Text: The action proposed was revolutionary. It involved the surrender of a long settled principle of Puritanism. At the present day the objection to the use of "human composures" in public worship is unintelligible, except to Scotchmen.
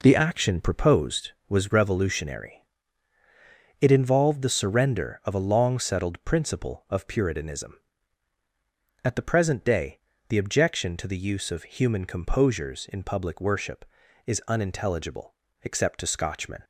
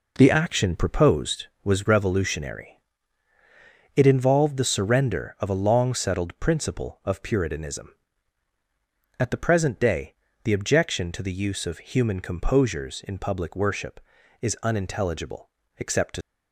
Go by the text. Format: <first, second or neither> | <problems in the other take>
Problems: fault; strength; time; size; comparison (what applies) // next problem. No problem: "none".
first | pauses between "day" and "the"; slight; at 10.1 s; 0.28 s long; slight in the first // stops before "Scotchmen"; at 16.2 s